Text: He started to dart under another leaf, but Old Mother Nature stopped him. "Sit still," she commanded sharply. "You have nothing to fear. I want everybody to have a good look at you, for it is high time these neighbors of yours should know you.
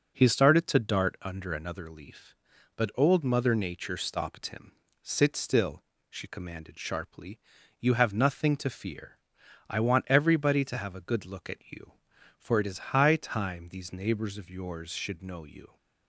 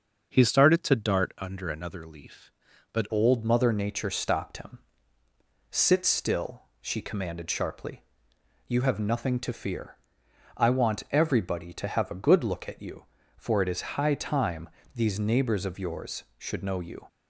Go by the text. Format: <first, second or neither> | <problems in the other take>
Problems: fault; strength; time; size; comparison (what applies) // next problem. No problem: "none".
first | starts louder than the rest; noticeable; until 1.3 s; 6 dB; noticeable in the first // changes voice at "Old"; from 3.1 s on; 13.9 s long // pauses between "time" and "these"; slight; at 14.6 s; 0.24 s long